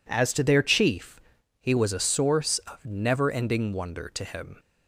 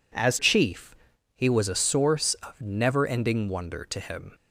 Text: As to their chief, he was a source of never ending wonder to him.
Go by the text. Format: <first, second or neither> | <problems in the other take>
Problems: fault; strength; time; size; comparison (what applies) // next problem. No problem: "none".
first | skips "to their"; at 0.3 s